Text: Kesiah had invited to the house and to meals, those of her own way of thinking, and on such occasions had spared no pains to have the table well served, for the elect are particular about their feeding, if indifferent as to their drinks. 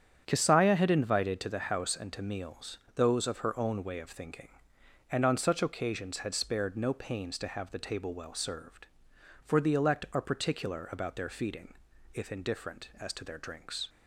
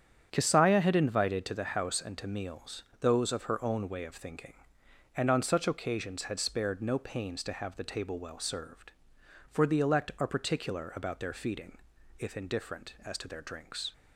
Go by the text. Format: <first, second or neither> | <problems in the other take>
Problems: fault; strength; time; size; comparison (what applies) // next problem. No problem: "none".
neither | starts louder than the rest; strong; the same in both